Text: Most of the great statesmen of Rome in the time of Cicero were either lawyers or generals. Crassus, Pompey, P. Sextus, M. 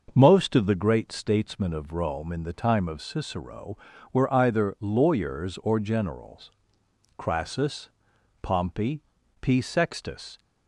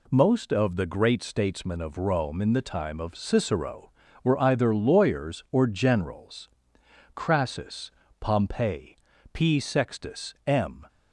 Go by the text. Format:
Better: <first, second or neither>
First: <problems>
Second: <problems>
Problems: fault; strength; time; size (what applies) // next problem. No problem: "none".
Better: second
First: starts louder than the rest; until 1.1 s; 6 dB // stops before "M"; at 10.3 s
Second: none